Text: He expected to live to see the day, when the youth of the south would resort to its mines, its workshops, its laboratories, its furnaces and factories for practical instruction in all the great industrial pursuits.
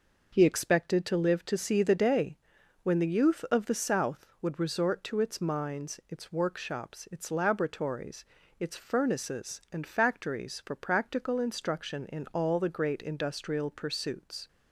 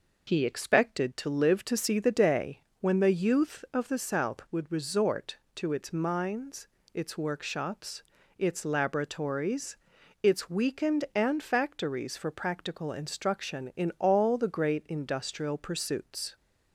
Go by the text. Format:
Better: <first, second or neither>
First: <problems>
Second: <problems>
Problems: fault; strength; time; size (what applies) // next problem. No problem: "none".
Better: first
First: none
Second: says "weakened" for "furnaces"; at 10.5 s